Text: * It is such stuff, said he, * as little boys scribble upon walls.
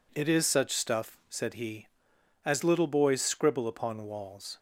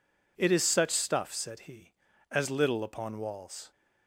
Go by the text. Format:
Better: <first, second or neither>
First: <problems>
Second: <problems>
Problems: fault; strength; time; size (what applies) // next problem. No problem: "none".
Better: first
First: none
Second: skips "boys scribble"; at 2.8 s